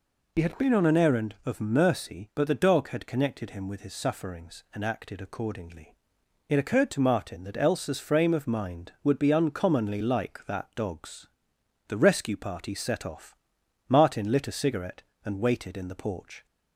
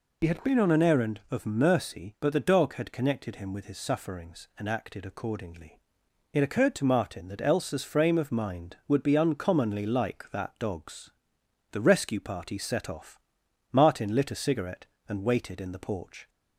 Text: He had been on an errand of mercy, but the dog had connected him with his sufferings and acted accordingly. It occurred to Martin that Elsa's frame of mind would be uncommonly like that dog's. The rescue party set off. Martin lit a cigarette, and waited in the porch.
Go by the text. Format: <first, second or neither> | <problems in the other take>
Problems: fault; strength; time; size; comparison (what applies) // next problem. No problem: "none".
neither | none